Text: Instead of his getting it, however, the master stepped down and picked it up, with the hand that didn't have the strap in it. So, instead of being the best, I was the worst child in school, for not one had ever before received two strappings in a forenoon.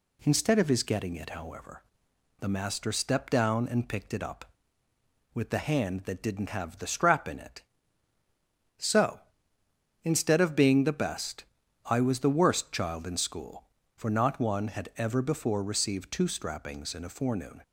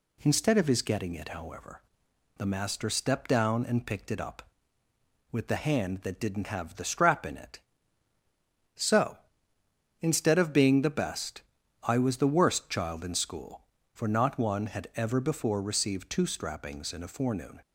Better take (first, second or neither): neither